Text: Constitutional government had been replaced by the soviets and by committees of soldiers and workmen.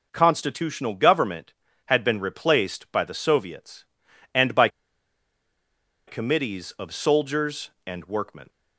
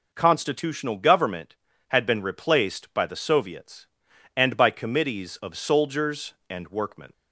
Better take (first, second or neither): second